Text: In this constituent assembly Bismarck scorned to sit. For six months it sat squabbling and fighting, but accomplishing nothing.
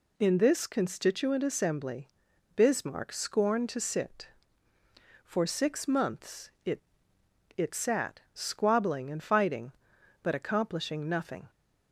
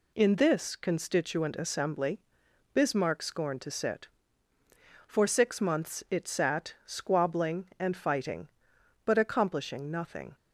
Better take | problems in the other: second | pauses between "assembly" and "Bismarck"; noticeable; at 2.0 s; 0.48 s long; noticeable in the second // says "it" twice; at 7.5 s

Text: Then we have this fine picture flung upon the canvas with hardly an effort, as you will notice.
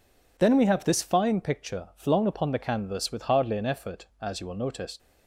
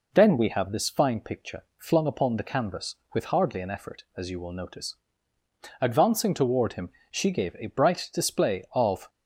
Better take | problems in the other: first | goes on to say "Advancing toward him she gave a bright display of"; strong; from 5.8 s on; 3.2 s long

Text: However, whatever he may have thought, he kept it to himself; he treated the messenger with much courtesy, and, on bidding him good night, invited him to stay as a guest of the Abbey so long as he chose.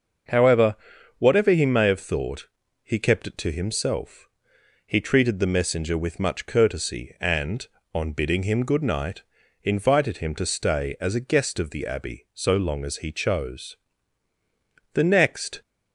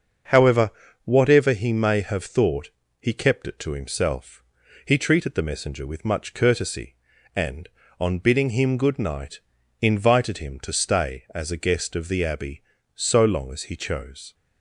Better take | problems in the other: second | starts louder than the rest; until 1.7 s; 6.5 dB; also in the second // goes on to say "The next"; noticeable; from 14.9 s on; 0.66 s long

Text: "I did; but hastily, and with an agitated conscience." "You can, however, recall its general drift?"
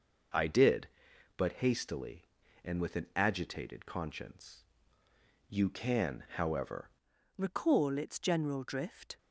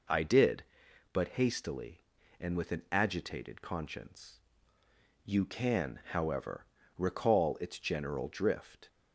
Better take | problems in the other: second | changes voice at "recall"; from 7.3 s on; 1.8 s long

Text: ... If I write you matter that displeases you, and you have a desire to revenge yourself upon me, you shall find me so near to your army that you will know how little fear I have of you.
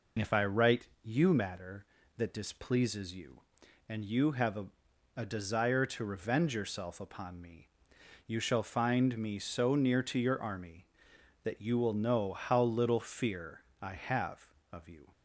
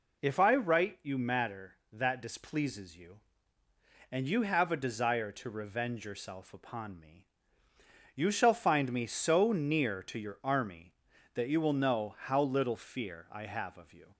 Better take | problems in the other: second | pauses between "write" and "you"; slight; at 0.8 s; 0.16 s long // says "a" twice; at 5.1 s // pauses between "fear" and "I"; slight; at 13.6 s; 0.18 s long

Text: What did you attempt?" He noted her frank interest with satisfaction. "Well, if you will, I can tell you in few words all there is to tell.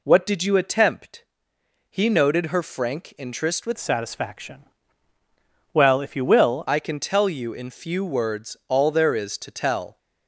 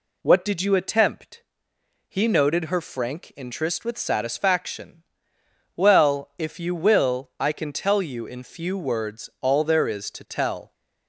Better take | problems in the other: second | changes voice from "satisfaction" to "will"; from 3.7 to 6.6 s; 2.9 s long

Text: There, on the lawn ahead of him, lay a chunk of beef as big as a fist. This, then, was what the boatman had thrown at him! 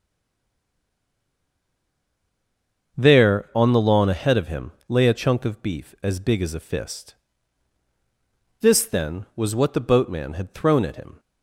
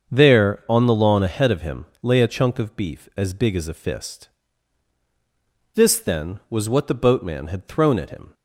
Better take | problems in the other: second | stays silent before the first word; strong; until 2.9 s; 2.9 s long // starts louder than the rest; until 4.0 s; 6.5 dB; also in the second

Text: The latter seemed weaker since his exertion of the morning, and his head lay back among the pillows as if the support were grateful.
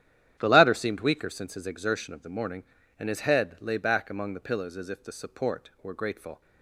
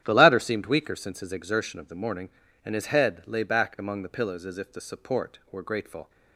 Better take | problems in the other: neither | starts louder than the rest; strong; the same in both

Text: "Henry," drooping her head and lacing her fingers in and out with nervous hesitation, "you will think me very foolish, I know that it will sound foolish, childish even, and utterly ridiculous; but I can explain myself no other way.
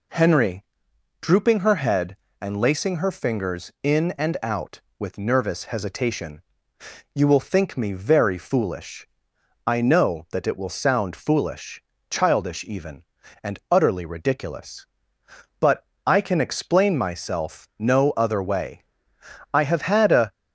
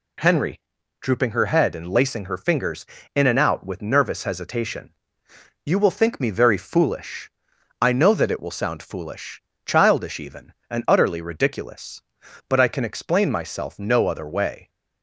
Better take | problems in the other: second | pauses between "but" and "I"; slight; at 15.8 s; 0.22 s long // goes on to say "I have had a"; noticeable; from 19.5 s on; 0.78 s long

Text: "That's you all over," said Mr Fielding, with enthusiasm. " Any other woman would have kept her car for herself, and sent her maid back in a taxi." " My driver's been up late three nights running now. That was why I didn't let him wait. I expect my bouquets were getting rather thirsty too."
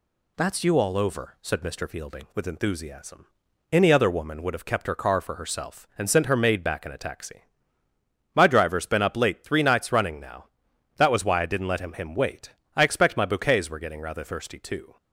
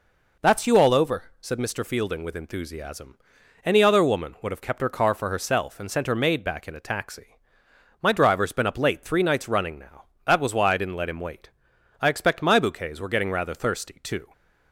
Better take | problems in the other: second | says "him" twice; at 11.9 s

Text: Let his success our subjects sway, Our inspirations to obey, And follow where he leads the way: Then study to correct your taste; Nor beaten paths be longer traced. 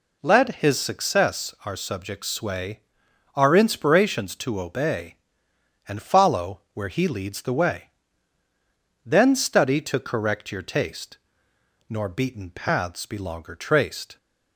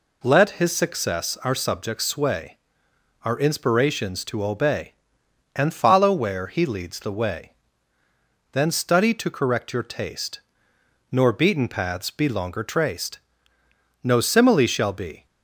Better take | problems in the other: first | goes on to say "No simile shall be"; noticeable; from 14.0 s on; 1.2 s long

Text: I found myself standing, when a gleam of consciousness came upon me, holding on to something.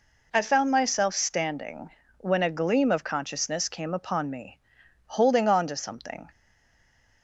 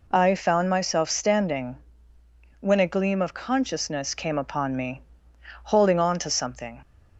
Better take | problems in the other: second | stays silent after the last word; slight; from 6.2 s on; 1.0 s long

